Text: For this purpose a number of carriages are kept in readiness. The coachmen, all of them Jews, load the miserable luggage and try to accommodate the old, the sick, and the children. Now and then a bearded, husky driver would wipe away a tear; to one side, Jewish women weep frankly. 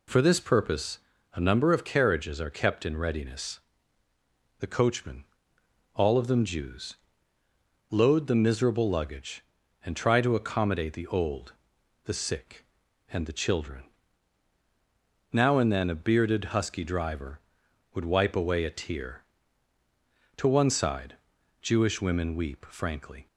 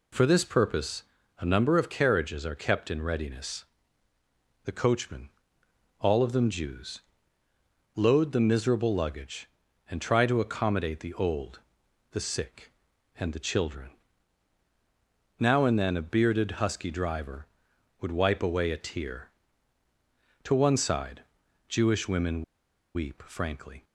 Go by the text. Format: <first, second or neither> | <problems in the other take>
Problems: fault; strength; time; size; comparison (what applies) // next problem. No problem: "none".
first | pauses between "purpose" and "a"; at 1.0 s; 0.38 s long; also in the first // pauses between "women" and "weep"; noticeable; at 22.4 s; 0.51 s long